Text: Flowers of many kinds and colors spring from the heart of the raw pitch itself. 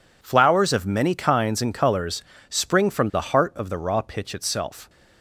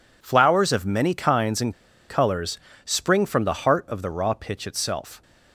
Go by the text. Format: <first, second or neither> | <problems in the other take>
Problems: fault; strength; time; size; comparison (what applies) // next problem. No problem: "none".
first | pauses between "and" and "colors"; at 1.7 s; 0.36 s long // pauses between "colors" and "spring"; slight; at 2.5 s; 0.26 s long; slight in the first